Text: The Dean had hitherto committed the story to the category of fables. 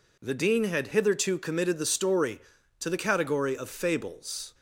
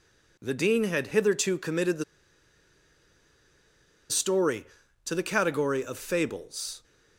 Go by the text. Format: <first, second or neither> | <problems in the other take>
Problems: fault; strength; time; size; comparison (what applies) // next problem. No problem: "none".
first | pauses between "the" and "story"; strong; at 2.0 s; 2.0 s long